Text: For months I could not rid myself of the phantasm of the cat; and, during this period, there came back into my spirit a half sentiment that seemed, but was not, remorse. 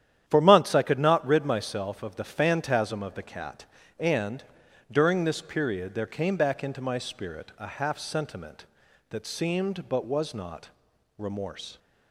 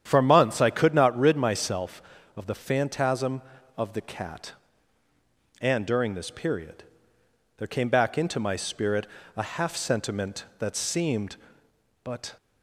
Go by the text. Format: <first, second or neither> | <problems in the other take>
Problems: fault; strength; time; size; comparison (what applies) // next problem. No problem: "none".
first | starts louder than the rest; strong; until 1.0 s; 9.5 dB; strong in the first // pauses between "spirit" and "a"; slight; at 9.0 s; 0.26 s long // stops before "was not remorse"; at 12.3 s